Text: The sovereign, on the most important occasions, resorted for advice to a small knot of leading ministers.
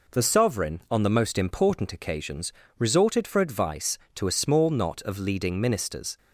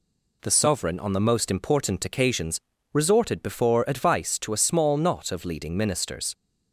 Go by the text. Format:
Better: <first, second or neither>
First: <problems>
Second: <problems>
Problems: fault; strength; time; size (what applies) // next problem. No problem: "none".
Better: first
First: none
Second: says "before" for "for"; at 3.4 s